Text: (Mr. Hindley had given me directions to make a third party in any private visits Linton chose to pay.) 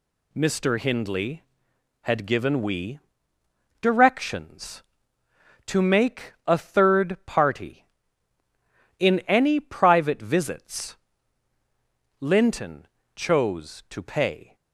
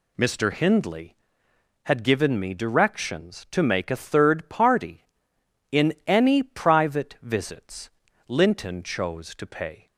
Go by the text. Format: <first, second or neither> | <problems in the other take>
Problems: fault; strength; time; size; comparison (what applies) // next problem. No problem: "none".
second | says "we" for "me"; at 2.6 s // pauses between "visits" and "Linton"; at 10.9 s; 1.2 s long; also in the second // pauses between "Linton" and "chose"; slight; at 12.8 s; 0.30 s long